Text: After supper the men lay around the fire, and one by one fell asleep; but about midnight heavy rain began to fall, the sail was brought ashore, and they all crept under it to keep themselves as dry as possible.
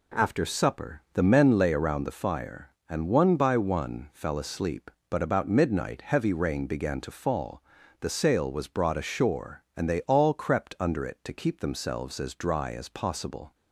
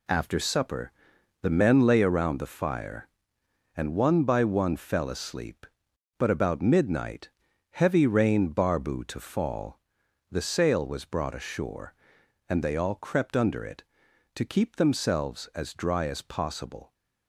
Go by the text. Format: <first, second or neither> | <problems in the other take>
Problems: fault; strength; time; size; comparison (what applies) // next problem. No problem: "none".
first | pauses between "supper" and "the"; noticeable; at 0.9 s; 0.50 s long // pauses between "midnight" and "heavy"; at 7.2 s; 0.42 s long // says "barbu" for "began"; at 8.4 s